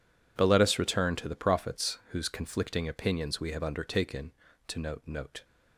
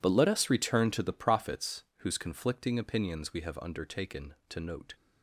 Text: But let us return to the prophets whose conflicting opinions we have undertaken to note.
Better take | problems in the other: second | says "note" twice; at 5.0 s

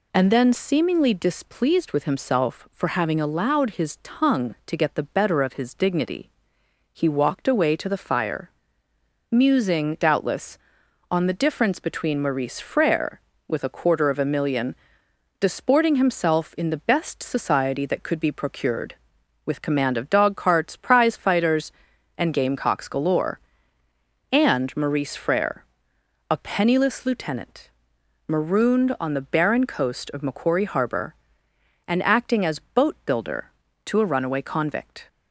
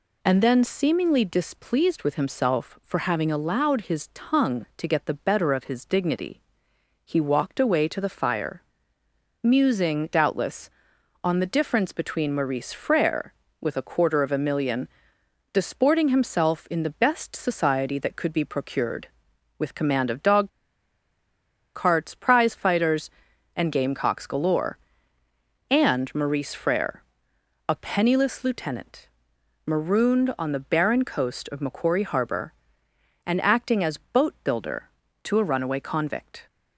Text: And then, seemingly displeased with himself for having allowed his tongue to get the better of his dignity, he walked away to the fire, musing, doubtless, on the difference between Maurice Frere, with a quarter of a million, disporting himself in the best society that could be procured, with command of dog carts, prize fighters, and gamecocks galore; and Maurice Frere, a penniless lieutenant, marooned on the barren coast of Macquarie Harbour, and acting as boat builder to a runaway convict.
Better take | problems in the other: first | pauses between "dog" and "carts"; strong; at 20.4 s; 1.2 s long

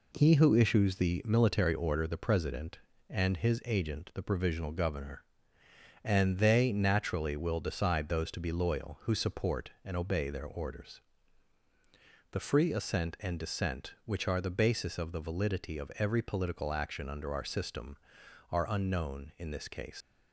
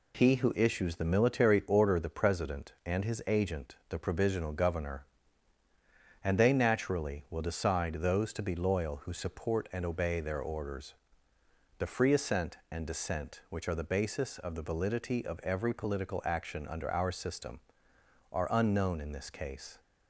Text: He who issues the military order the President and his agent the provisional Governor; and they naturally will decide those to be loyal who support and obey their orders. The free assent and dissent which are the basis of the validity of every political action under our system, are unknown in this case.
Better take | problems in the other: second | leaves "case" unfinished; at 20.0 s; 125 ms

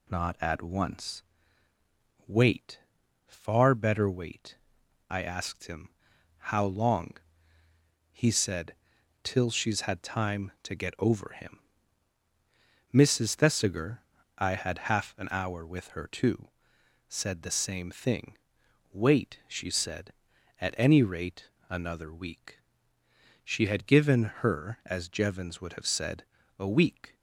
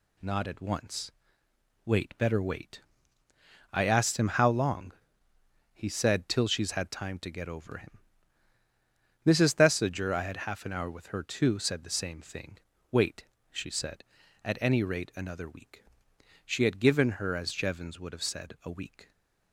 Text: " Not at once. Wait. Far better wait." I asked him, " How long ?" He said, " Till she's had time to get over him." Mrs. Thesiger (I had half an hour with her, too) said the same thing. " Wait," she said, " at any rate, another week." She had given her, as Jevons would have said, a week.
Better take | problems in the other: first | skips "Far"; at 2.1 s

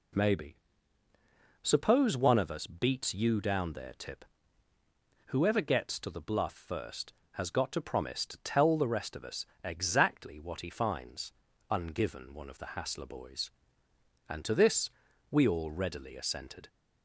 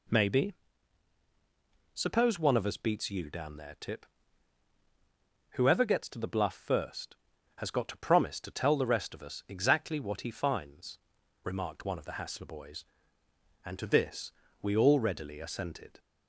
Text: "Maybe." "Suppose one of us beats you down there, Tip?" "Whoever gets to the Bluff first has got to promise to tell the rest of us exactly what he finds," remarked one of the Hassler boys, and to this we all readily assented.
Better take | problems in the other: second | pauses between "us" and "exactly"; slight; at 9.4 s; 0.18 s long // says "ungiven" for "remarked"; at 11.6 s // pauses between "this" and "we"; at 14.8 s; 0.42 s long; slight in the second

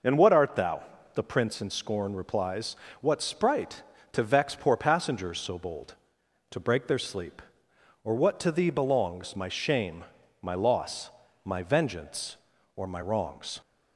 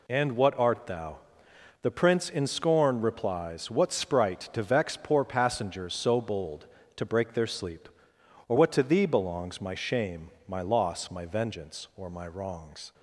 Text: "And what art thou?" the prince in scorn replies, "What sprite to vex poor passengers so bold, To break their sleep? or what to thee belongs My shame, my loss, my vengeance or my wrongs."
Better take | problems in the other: neither | none

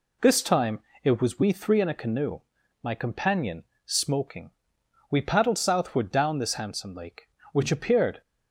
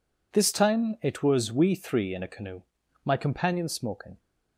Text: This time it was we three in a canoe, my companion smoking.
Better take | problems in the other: second | pauses between "time" and "it"; slight; at 0.8 s; 0.24 s long // pauses between "companion" and "smoking"; slight; at 3.6 s; 0.22 s long // goes on to say "We paddled southward down this handsome lake which appeared"; strong; from 5.1 s on; 3.1 s long

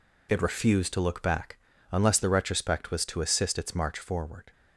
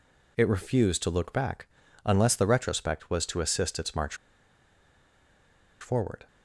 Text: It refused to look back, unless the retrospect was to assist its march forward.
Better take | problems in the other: first | pauses between "march" and "forward"; strong; at 4.1 s; 1.6 s long

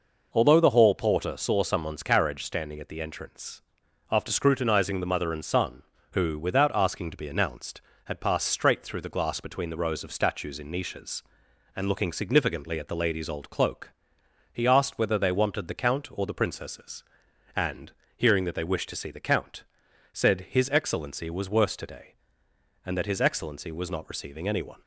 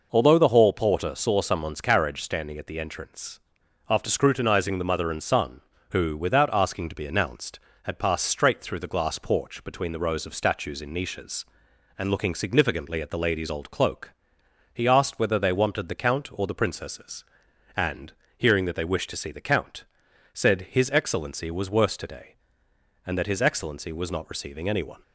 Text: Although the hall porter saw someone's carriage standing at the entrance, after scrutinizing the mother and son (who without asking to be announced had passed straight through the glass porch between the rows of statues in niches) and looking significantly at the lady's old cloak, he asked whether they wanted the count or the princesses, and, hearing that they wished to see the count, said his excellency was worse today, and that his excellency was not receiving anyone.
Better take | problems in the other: second | skips "porch"; at 9.4 s

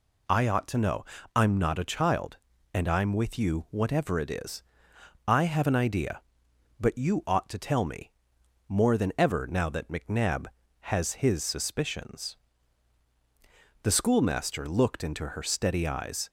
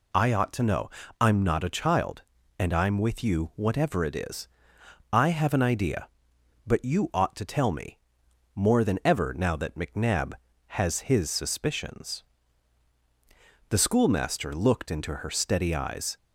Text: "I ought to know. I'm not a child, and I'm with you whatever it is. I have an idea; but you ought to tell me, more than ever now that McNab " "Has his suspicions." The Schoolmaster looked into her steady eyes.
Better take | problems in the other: neither | none

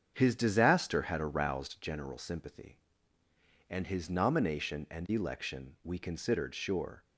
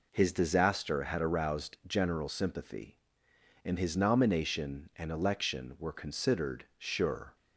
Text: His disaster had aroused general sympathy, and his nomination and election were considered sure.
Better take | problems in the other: second | starts louder than the rest; strong; until 1.1 s; 7.5 dB // says "we" for "were"; at 5.8 s

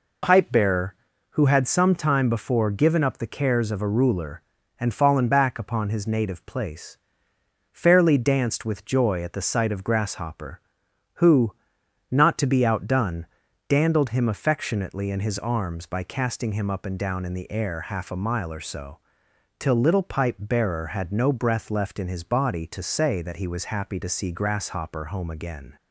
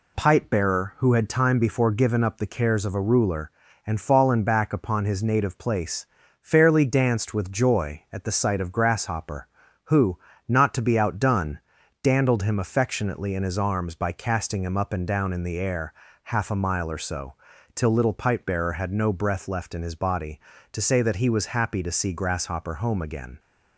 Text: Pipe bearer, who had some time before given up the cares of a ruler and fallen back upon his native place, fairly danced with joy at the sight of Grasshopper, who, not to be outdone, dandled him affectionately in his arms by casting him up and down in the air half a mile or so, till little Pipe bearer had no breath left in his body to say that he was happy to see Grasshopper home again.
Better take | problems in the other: first | skips "some"; at 1.2 s // pauses between "air" and "half"; slight; at 15.9 s; 0.32 s long

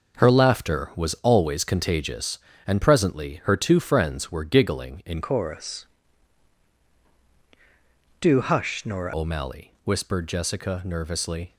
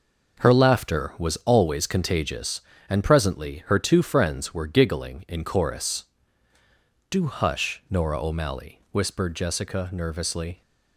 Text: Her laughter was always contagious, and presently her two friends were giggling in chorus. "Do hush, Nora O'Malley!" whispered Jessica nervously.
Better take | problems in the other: second | changes voice from "chorus" to "Nora"; from 5.2 to 9.1 s; 3.9 s long

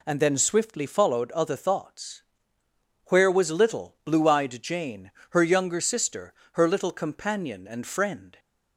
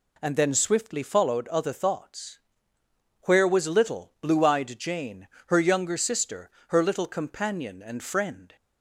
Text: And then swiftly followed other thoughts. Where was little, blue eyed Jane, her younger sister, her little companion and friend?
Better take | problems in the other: neither | none

